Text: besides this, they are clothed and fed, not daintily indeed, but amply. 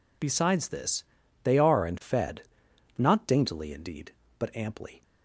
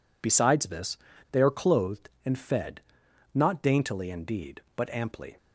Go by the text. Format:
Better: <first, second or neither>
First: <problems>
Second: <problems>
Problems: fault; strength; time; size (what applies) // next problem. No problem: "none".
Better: second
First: skips "clothed"; at 1.8 s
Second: none